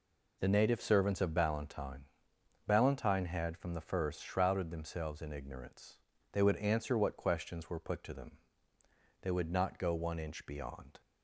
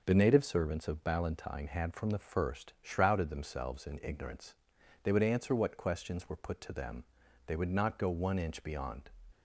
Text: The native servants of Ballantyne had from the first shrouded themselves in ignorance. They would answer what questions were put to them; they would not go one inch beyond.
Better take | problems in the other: second | says "Ballantyne" twice; at 2.6 s

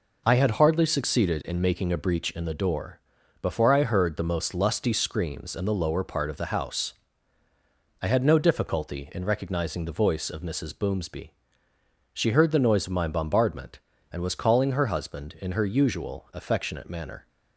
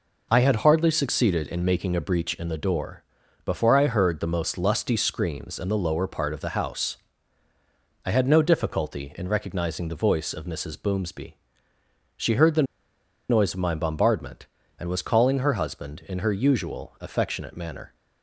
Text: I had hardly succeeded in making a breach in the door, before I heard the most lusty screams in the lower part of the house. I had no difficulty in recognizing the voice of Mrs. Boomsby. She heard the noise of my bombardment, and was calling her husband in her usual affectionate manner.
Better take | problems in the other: first | pauses between "the" and "noise"; noticeable; at 12.6 s; 0.66 s long

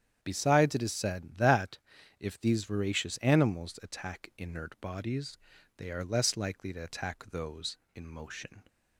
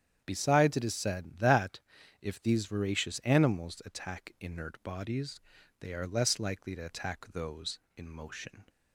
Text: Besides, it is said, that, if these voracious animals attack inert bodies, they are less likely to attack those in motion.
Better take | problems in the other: neither | starts louder than the rest; strong; the same in both

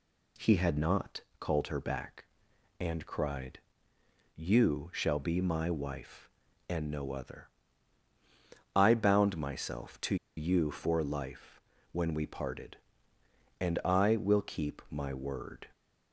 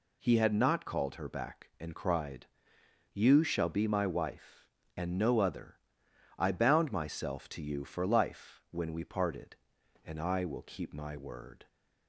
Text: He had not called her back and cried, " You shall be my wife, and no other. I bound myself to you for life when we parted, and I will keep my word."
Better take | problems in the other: second | pauses between "not" and "called"; slight; at 1.2 s; 0.18 s long // pauses between "to" and "you"; slight; at 10.1 s; 0.22 s long // pauses between "life" and "when"; slight; at 11.5 s; 0.32 s long

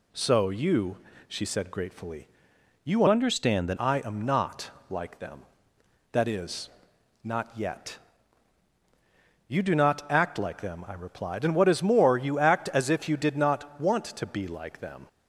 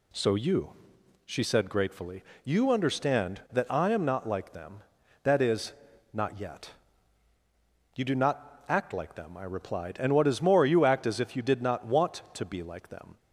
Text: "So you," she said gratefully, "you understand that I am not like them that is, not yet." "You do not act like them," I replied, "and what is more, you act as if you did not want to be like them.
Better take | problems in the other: second | changes voice from "understand" to "that"; from 3.0 to 3.7 s; 0.7 s long // pauses between "not" and "like"; slight; at 4.6 s; 0.20 s long

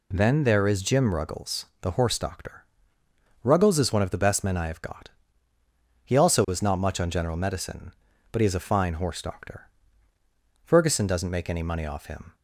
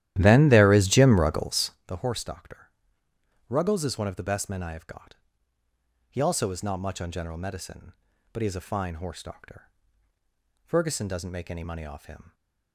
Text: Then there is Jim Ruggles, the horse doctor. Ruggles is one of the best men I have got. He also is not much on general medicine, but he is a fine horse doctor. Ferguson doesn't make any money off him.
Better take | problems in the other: first | starts louder than the rest; strong; until 1.9 s; 13 dB

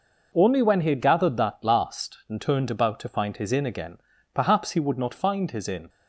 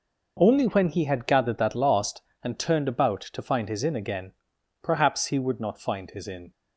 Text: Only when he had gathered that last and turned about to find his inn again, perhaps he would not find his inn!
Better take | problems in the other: neither | none

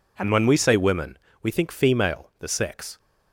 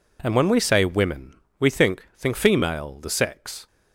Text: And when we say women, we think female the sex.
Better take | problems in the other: first | says "think" twice; at 2.1 s

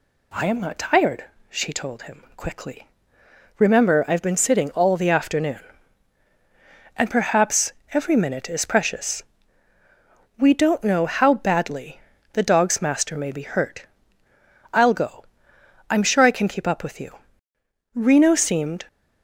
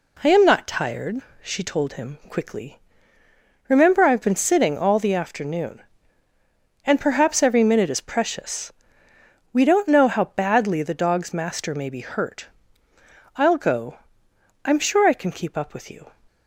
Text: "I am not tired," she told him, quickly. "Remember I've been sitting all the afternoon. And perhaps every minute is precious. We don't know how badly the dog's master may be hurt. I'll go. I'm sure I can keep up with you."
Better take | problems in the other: second | pauses between "perhaps" and "every"; slight; at 7.7 s; 0.20 s long // pauses between "badly" and "the"; slight; at 12.0 s; 0.32 s long // goes on to say "Reno seemed"; noticeable; from 17.9 s on; 0.92 s long

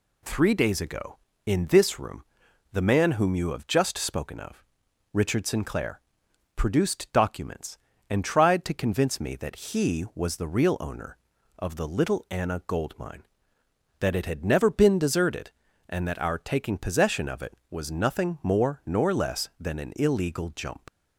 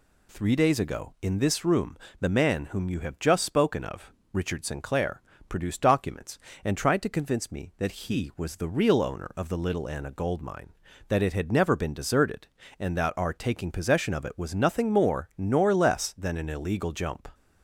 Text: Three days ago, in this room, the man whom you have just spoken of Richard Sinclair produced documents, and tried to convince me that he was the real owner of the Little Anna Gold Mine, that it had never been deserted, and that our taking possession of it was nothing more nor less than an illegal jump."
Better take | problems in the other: second | pauses between "of" and "Richard"; noticeable; at 4.6 s; 0.48 s long; slight in the second // pauses between "Sinclair" and "produced"; noticeable; at 5.9 s; 0.56 s long; slight in the second // leaves "jump" unfinished; at 20.8 s; 55 ms

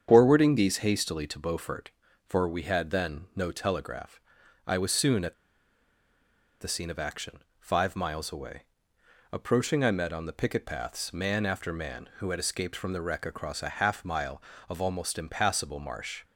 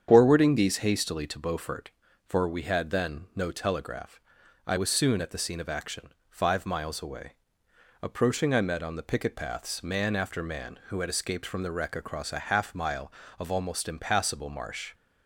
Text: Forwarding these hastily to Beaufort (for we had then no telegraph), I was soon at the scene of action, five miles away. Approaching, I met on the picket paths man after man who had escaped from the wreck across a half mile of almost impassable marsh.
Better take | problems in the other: second | starts louder than the rest; strong; until 1.1 s; 8 dB; strong in the second // pauses between "at" and "the"; strong; at 5.3 s; 1.2 s long

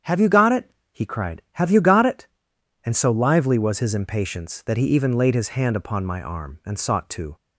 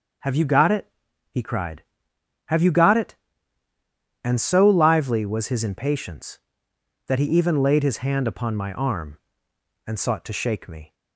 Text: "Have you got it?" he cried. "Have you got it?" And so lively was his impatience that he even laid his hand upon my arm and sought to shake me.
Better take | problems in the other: second | starts louder than the rest; strong; until 1.2 s; 8 dB // stops before "shake me"; at 7.3 s

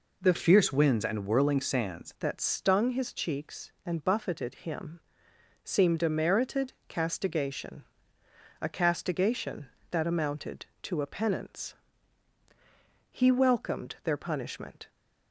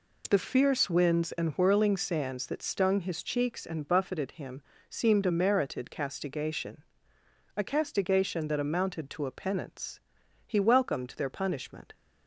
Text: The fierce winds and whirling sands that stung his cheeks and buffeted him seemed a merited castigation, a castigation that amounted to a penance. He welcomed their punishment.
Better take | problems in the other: second | changes voice from "fierce" to "sands"; from 0.3 to 2.1 s; 1.8 s long // pauses between "him" and "seemed"; noticeable; at 4.9 s; 0.64 s long; slight in the second // pauses between "merited" and "castigation"; slight; at 6.7 s; 0.16 s long

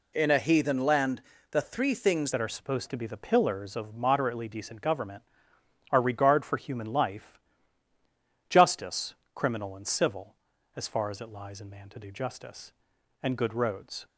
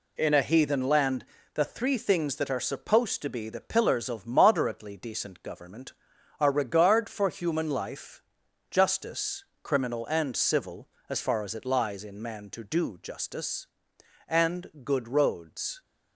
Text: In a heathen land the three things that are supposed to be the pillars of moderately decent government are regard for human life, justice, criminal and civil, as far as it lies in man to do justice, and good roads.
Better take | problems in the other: second | pauses between "land" and "the"; slight; at 1.2 s; 0.28 s long; slight in the second // changes voice at "that"; from 2.3 s on; 11.7 s long

